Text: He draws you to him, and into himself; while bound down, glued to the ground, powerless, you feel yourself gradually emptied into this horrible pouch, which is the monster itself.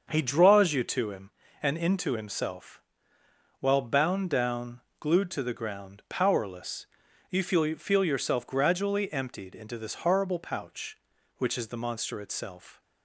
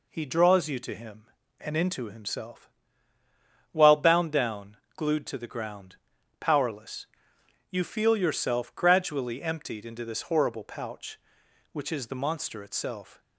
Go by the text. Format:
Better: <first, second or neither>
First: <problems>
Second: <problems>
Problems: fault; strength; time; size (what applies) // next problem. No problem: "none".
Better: second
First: starts louder than the rest; until 1.1 s; 6.5 dB // says "feel" twice; at 7.7 s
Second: none